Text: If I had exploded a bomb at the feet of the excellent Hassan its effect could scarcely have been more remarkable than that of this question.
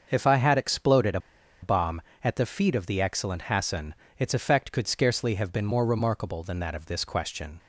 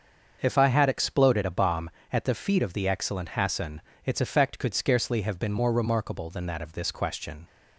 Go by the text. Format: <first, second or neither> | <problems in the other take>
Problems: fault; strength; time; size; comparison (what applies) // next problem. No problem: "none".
second | starts louder than the rest; until 1.1 s; 6.5 dB; also in the second // pauses between "a" and "bomb"; at 1.1 s; 0.42 s long // pauses between "Hassan" and "its"; slight; at 3.9 s; 0.24 s long; slight in the second